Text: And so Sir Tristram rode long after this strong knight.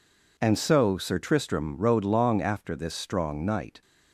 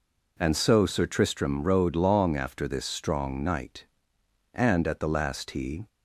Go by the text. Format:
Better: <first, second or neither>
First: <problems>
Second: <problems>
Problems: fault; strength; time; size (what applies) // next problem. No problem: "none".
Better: first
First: none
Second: goes on to say "And at the last he"; from 4.5 s on; 1.3 s long